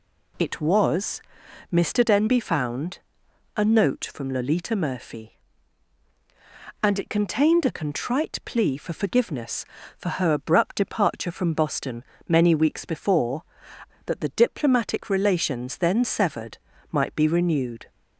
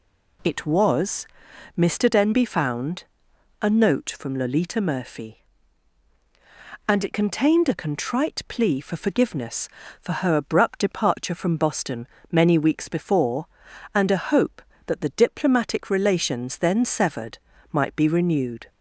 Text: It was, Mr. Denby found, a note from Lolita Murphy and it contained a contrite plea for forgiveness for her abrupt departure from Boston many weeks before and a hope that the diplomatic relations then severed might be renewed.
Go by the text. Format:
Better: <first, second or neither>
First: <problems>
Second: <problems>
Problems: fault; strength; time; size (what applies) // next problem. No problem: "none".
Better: second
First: pauses between "Boston" and "many"; slight; at 12.0 s; 0.24 s long // skips "and a hope"; at 13.7 s // pauses between "severed" and "might"; slight; at 16.5 s; 0.36 s long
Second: pauses between "Boston" and "many"; slight; at 12.0 s; 0.24 s long // pauses between "severed" and "might"; slight; at 17.3 s; 0.36 s long